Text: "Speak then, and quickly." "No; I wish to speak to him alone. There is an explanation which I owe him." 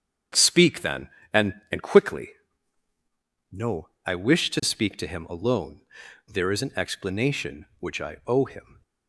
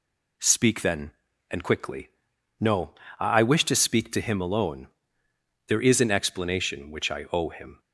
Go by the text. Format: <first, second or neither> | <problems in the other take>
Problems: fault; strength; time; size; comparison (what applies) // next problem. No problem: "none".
second | starts louder than the rest; strong; until 1.5 s; 8 dB // says "and" twice; at 1.6 s